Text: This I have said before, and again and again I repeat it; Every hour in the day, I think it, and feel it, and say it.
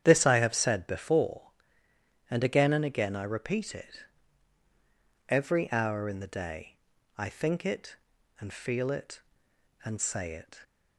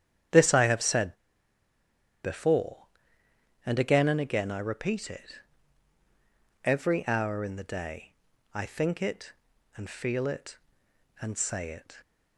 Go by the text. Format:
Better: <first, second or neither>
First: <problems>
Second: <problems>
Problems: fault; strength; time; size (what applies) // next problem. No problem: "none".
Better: first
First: starts louder than the rest; strong; until 1.0 s; 9.5 dB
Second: starts louder than the rest; strong; until 2.4 s; 9.5 dB // pauses between "said" and "before"; at 1.1 s; 1.0 s long